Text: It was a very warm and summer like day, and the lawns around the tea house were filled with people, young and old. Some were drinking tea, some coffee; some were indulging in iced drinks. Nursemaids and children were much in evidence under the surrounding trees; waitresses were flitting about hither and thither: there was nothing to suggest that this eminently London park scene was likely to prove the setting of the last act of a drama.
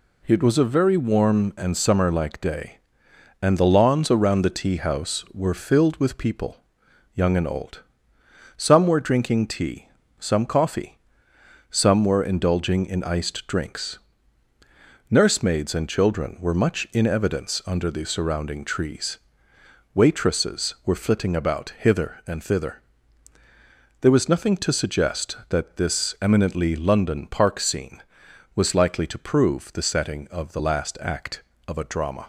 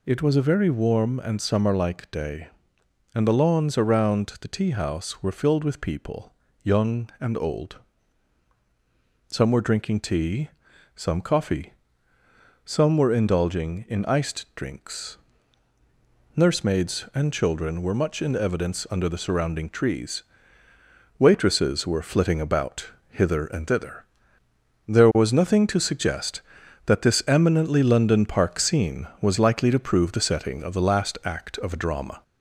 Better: first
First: none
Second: gets louder; slight; throughout; 2.5 dB // pauses between "about" and "hither"; slight; at 22.9 s; 0.18 s long

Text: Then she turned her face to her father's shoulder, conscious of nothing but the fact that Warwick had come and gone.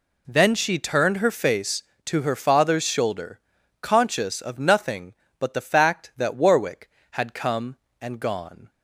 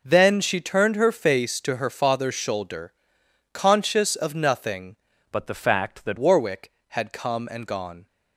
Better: first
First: none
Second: changes voice from "but" to "that"; from 5.3 to 6.1 s; 0.8 s long

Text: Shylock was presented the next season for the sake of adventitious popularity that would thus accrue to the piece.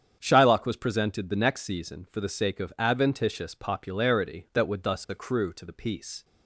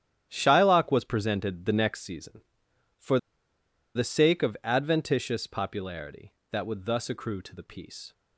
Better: first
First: starts louder than the rest; strong; until 1.2 s; 8 dB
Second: starts louder than the rest; strong; until 1.3 s; 10.5 dB // pauses between "for" and "the"; noticeable; at 3.1 s; 0.78 s long

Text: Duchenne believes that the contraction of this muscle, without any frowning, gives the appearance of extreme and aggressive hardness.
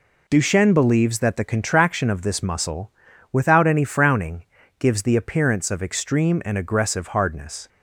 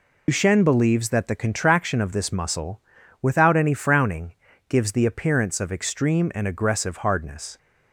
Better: first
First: none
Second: loses the start of "Duchenne"; at 0.2 s; 90 ms

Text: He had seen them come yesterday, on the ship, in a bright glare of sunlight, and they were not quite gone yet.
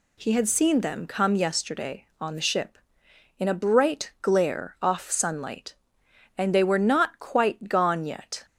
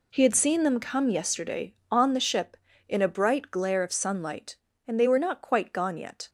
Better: second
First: says "off" for "of"; at 4.8 s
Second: none

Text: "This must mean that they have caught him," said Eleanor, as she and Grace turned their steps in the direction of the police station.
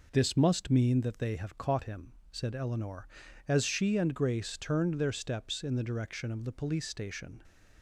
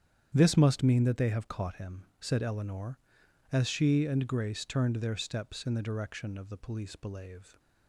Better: first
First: none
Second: starts louder than the rest; strong; until 1.3 s; 9 dB // says "belave" for "station"; at 6.9 s

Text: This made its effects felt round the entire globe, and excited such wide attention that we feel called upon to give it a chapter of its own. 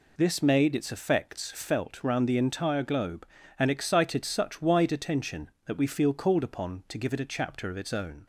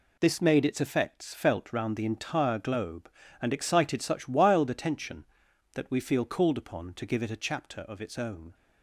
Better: first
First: none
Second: says "wild" for "wide"; at 4.2 s

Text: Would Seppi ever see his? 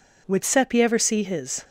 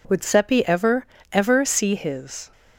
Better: first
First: none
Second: says "ever" twice; at 1.3 s

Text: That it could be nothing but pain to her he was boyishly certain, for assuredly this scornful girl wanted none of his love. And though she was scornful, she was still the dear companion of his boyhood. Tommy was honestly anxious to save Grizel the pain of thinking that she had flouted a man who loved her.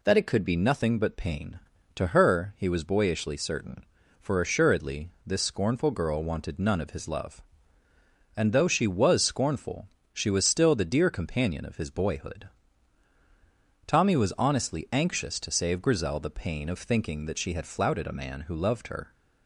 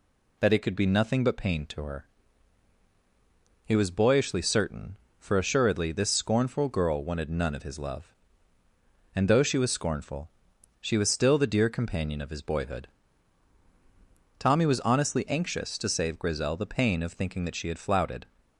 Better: first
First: none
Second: pauses between "her" and "he"; strong; at 2.0 s; 1.5 s long // stops before "a man who loved her"; at 18.3 s

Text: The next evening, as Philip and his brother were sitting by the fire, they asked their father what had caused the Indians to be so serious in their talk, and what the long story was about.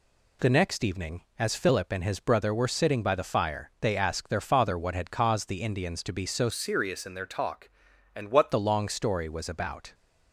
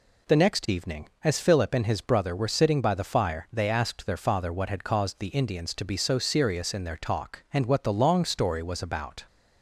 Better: second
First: changes voice from "serious" to "what"; from 6.4 to 8.5 s; 2.1 s long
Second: none

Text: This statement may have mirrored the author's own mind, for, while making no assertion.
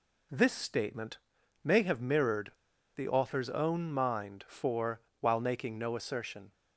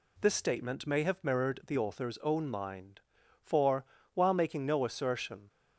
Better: second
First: pauses between "statement" and "may"; at 1.1 s; 0.44 s long // pauses between "mirrored" and "the"; at 2.5 s; 0.42 s long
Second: none

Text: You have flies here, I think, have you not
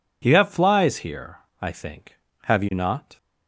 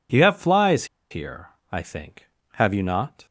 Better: first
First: none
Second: pauses between "flies" and "here"; slight; at 0.8 s; 0.24 s long

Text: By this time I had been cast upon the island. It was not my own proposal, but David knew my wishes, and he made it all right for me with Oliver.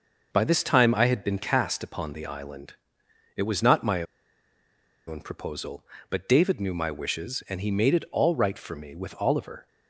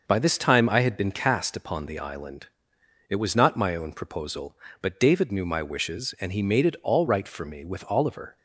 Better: second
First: pauses between "my" and "own"; at 4.0 s; 1.0 s long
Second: none

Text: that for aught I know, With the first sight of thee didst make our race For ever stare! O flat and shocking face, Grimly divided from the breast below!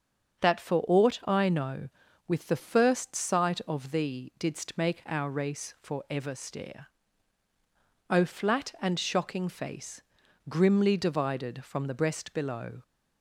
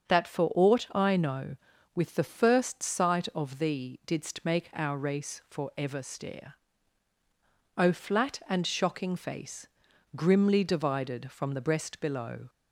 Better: neither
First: starts louder than the rest; until 1.5 s; 6.5 dB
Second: starts louder than the rest; until 1.1 s; 6.5 dB

